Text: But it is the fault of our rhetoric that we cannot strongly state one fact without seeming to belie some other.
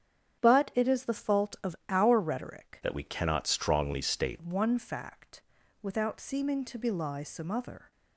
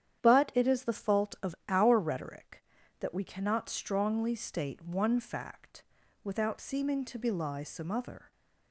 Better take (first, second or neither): second